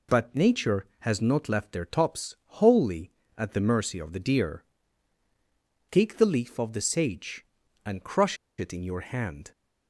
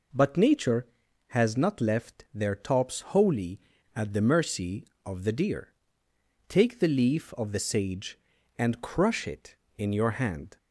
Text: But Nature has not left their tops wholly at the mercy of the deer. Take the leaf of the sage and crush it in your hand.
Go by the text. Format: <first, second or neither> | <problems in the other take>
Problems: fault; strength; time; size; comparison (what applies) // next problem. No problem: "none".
second | pauses between "tops" and "wholly"; slight; at 2.3 s; 0.24 s long // pauses between "crush" and "it"; slight; at 8.3 s; 0.24 s long